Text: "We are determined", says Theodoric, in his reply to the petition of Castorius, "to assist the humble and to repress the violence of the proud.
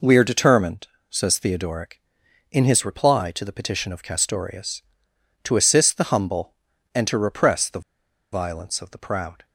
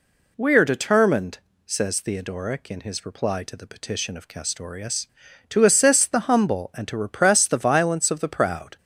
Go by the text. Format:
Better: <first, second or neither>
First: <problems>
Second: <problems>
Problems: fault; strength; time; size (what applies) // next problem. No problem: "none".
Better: second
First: pauses between "the" and "violence"; noticeable; at 7.8 s; 0.52 s long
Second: none